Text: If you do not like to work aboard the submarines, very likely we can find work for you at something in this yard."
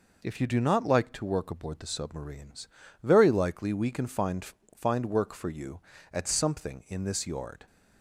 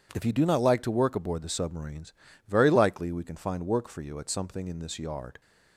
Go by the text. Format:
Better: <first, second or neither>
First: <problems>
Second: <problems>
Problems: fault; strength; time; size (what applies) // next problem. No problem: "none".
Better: second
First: says "find" twice; at 4.7 s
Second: none